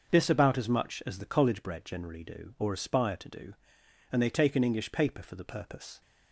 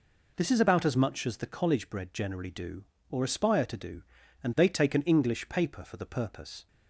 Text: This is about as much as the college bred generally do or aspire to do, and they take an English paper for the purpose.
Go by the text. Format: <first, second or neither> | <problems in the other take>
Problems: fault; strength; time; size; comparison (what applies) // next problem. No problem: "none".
second | starts louder than the rest; noticeable; until 1.1 s; 6 dB // skips "is"; at 0.2 s